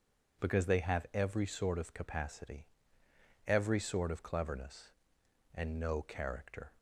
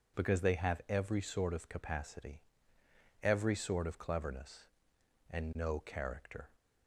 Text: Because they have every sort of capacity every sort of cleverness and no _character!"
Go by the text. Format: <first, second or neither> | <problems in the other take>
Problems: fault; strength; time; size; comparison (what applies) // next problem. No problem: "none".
neither | pauses between "capacity" and "every"; noticeable; the same in both